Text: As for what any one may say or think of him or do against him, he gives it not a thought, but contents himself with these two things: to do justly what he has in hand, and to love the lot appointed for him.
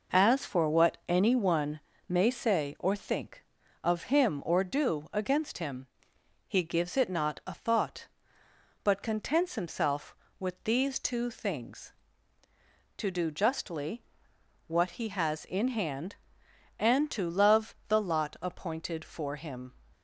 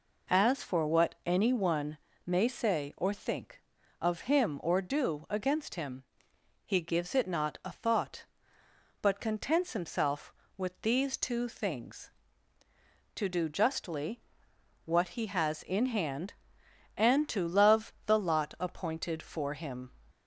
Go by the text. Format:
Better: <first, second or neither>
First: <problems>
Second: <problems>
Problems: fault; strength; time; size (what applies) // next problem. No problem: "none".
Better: second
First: gets quieter; noticeable; throughout; 4.5 dB // pauses between "one" and "may"; slight; at 1.7 s; 0.30 s long // pauses between "justly" and "what"; noticeable; at 14.0 s; 0.64 s long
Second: pauses between "one" and "may"; slight; at 1.9 s; 0.30 s long // pauses between "justly" and "what"; noticeable; at 14.1 s; 0.64 s long